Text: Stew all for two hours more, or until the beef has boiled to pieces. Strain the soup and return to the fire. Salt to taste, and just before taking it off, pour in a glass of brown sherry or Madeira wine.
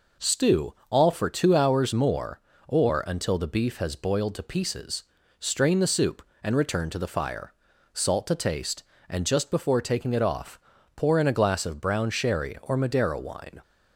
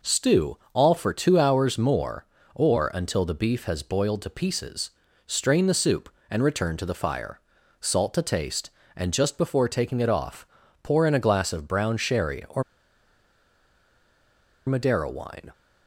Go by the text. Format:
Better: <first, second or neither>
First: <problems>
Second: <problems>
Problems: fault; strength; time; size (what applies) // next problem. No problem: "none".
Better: first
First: none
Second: pauses between "or" and "Madeira"; strong; at 12.6 s; 2.0 s long